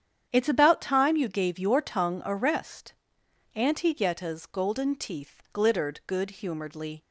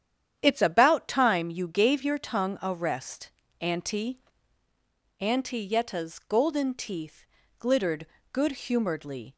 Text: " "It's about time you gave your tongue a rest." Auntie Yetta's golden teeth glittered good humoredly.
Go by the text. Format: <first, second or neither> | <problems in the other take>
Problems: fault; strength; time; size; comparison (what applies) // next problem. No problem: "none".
first | starts louder than the rest; strong; until 1.4 s; 9.5 dB; strong in the first // says "Auntie" twice; at 5.1 s // pauses between "teeth" and "glittered"; slight; at 7.2 s; 0.32 s long // pauses between "glittered" and "good"; slight; at 8.0 s; 0.26 s long